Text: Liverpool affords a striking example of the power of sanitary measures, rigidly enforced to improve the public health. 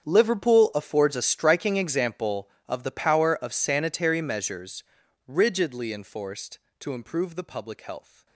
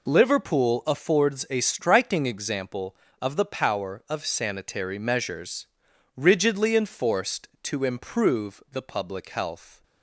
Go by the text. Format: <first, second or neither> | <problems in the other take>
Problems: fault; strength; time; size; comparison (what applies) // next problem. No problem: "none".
second | gets quieter; strong; throughout; 18 dB